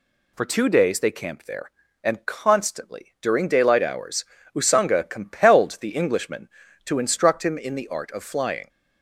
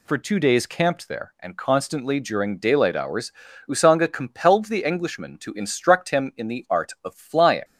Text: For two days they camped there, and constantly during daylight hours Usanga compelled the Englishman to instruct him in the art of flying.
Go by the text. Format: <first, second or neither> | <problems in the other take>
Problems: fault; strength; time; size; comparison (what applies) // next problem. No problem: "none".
first | skips "they"; at 0.6 s // pauses between "hours" and "Usanga"; slight; at 3.3 s; 0.36 s long; slight in the first